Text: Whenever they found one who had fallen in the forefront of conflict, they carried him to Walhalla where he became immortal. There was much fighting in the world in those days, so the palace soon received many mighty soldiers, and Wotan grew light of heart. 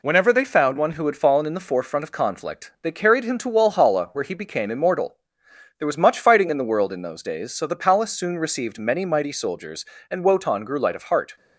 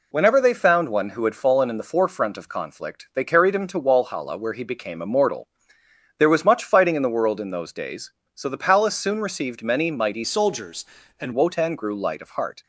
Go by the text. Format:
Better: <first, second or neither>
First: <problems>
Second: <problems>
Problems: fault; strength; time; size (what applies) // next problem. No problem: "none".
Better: first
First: none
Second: changes voice from "soldiers" to "and"; from 10.2 to 11.3 s; 1.1 s long